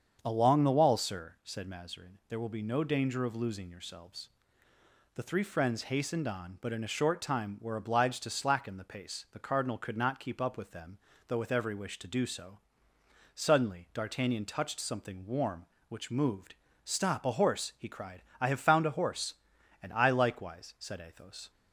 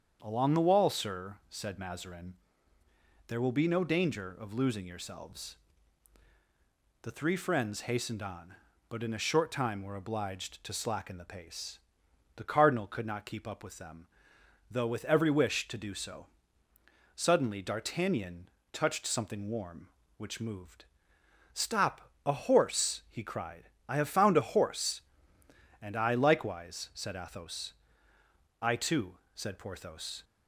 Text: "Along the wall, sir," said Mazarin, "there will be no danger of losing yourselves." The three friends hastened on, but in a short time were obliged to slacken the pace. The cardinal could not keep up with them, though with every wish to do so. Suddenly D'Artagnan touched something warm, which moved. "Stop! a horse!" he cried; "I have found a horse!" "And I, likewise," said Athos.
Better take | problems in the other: first | starts louder than the rest; strong; until 1.2 s; 7 dB; strong in the first // pauses between "D'Artagnan" and "touched"; slight; at 18.4 s; 0.22 s long // goes on to say "I too said Porthos"; from 28.5 s on; 1.6 s long

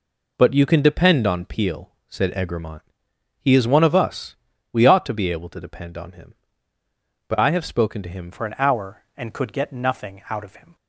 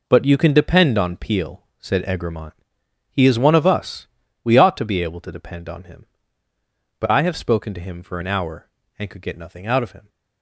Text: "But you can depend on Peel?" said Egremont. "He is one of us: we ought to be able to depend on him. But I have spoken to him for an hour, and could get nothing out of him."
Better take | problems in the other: second | changes voice at "for"; from 8.3 s on; 2.4 s long

